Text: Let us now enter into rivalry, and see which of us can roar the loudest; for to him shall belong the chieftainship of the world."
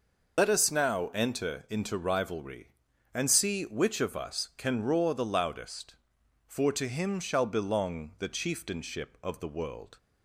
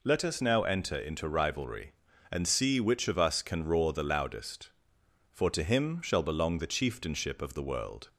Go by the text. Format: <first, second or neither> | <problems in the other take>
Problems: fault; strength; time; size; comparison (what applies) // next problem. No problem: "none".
second | loses the start of "Let"; at 0.3 s; 65 ms